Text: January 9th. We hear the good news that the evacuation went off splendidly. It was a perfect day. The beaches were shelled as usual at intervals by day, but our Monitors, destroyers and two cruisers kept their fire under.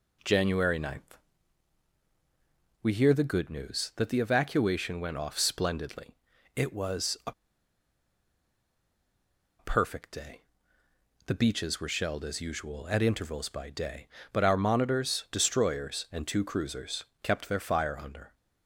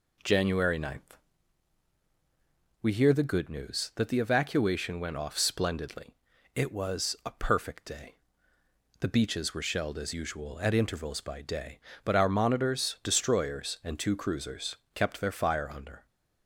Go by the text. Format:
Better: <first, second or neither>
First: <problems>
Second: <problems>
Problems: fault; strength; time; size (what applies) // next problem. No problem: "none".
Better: second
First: pauses between "a" and "perfect"; strong; at 7.3 s; 2.2 s long // pauses between "cruisers" and "kept"; slight; at 17.0 s; 0.18 s long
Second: pauses between "cruisers" and "kept"; slight; at 14.7 s; 0.18 s long